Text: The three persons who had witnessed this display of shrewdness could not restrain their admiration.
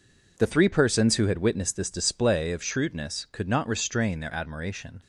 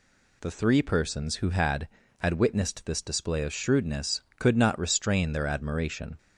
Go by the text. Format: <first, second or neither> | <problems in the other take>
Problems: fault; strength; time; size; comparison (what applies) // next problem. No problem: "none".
first | says "had" twice; at 2.1 s